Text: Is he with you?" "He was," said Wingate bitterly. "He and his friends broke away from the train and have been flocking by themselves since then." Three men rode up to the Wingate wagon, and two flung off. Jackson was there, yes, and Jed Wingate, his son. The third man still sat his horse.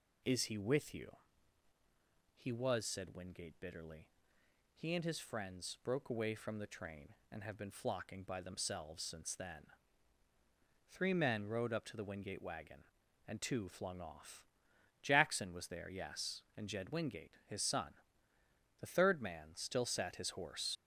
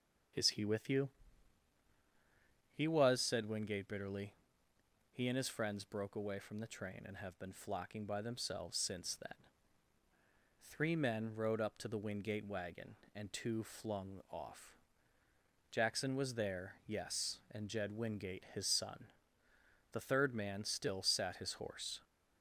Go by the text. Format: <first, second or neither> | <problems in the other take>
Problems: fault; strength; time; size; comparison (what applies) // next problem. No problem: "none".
second | leaves "horse" unfinished; at 20.7 s; 75 ms